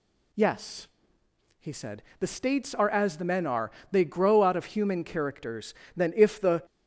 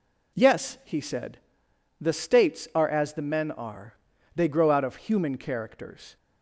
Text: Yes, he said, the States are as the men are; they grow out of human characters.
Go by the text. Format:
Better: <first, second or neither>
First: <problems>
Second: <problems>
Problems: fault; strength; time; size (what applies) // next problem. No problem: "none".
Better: second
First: goes on to say "Then if the"; noticeable; from 5.9 s on; 0.70 s long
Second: none